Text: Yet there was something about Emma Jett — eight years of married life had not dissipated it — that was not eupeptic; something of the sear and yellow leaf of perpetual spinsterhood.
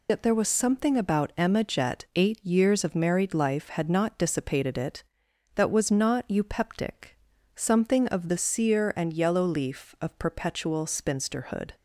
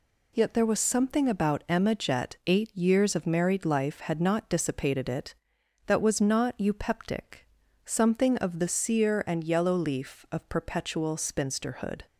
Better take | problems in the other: second | loses the start of "Yet"; at 0.0 s; 70 ms

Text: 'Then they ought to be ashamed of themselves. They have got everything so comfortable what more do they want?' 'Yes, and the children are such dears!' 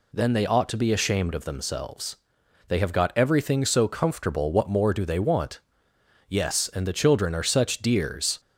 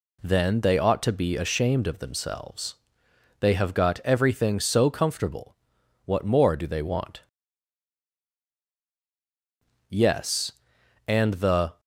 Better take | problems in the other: first | pauses between "comfortable" and "what"; noticeable; at 5.5 s; 0.48 s long // stops before "children are such dears"; at 11.7 s

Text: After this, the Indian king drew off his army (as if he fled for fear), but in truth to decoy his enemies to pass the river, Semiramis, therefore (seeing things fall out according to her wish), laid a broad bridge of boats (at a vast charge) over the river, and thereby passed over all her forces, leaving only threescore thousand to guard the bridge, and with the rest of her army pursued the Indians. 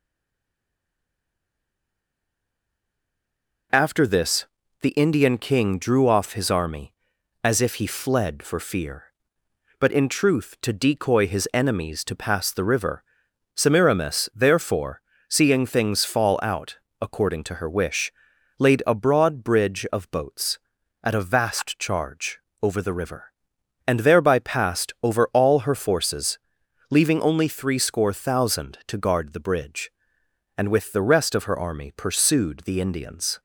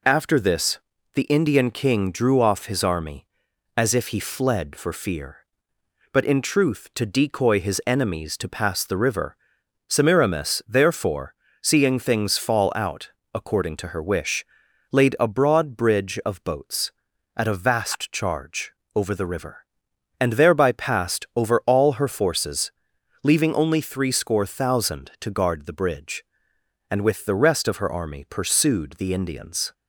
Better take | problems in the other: second | stays silent before the first word; strong; until 3.7 s; 3.7 s long // pauses between "out" and "according"; slight; at 16.7 s; 0.22 s long; slight in the second

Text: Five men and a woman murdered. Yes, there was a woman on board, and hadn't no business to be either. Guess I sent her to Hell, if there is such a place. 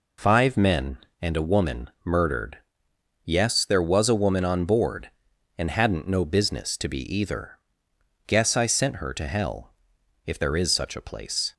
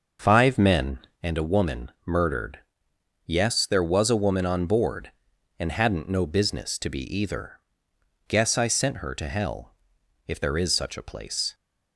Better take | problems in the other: first | starts louder than the rest; noticeable; until 1.3 s; 6 dB // pauses between "be" and "either"; slight; at 7.0 s; 0.16 s long; slight in the first

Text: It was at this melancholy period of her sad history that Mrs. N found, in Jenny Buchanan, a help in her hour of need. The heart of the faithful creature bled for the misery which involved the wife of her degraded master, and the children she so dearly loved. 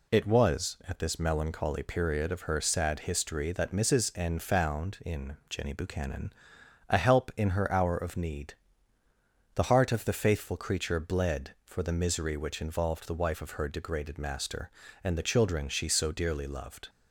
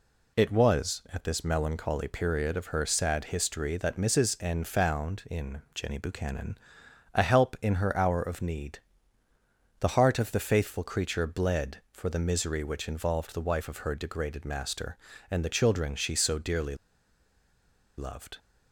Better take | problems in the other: first | pauses between "dearly" and "loved"; at 16.7 s; 1.2 s long

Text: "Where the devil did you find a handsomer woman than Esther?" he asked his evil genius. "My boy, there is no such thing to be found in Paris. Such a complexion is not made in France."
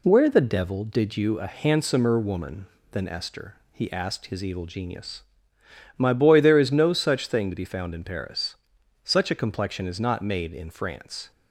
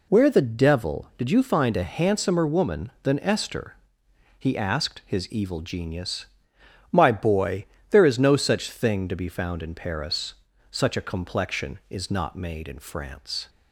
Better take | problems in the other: second | skips "find"; at 1.3 s

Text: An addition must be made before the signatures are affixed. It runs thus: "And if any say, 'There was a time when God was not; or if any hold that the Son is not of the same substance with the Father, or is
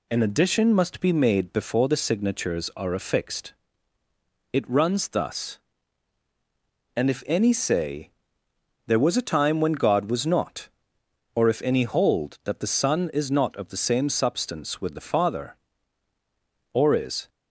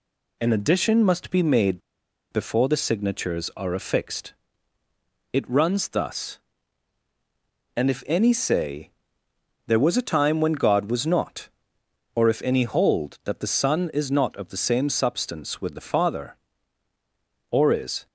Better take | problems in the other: first | pauses between "made" and "before"; noticeable; at 1.8 s; 0.51 s long

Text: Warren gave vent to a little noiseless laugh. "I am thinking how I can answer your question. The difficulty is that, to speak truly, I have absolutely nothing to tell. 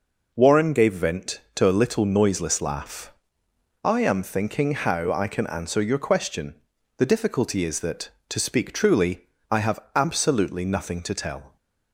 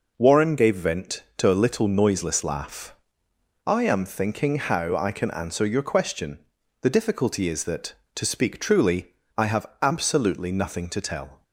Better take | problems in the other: neither | pauses between "have" and "absolutely"; slight; the same in both

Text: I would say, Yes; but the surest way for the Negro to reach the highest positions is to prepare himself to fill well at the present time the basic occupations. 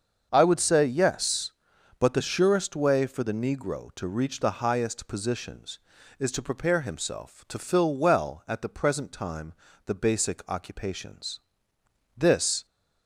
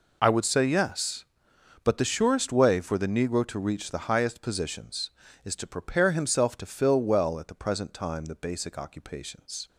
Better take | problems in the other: second | starts louder than the rest; until 1.3 s; 7 dB // pauses between "time" and "the"; slight; at 9.5 s; 0.32 s long // goes on to say "This"; from 12.1 s on; 0.50 s long

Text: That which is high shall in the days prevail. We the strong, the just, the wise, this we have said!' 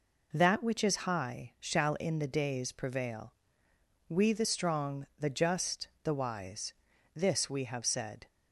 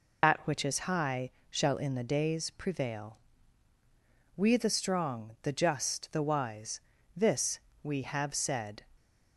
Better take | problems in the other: first | loses the start of "That"; at 0.2 s; 100 ms // pauses between "high" and "shall"; slight; at 1.2 s; 0.20 s long // pauses between "this" and "we"; slight; at 7.5 s; 0.22 s long

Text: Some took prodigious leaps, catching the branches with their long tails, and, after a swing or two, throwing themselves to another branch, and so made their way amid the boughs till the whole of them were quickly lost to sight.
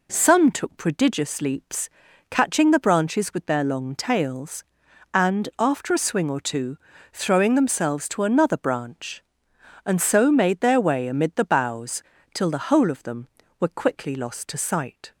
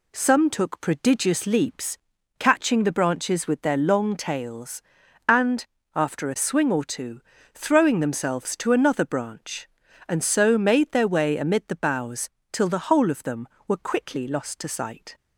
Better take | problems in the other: neither | pauses between "boughs" and "till"; slight; the same in both

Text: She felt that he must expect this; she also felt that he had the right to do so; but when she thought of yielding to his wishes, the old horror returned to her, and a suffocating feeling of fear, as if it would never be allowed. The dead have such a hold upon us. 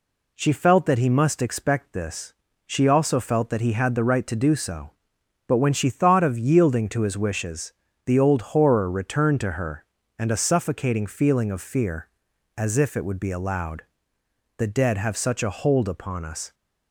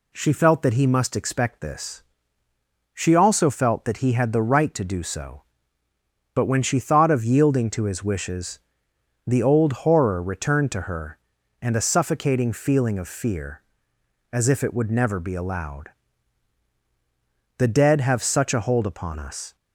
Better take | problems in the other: second | skips "never"; at 13.1 s

